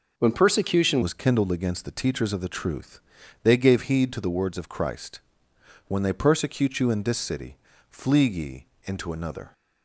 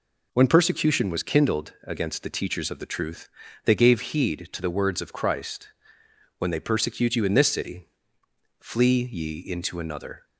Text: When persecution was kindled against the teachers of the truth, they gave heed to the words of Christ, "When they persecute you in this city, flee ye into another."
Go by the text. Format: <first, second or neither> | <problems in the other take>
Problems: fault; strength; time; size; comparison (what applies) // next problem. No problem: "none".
second | changes voice at "was"; from 1.0 s on; 8.5 s long // pauses between "ye" and "into"; slight; at 8.6 s; 0.18 s long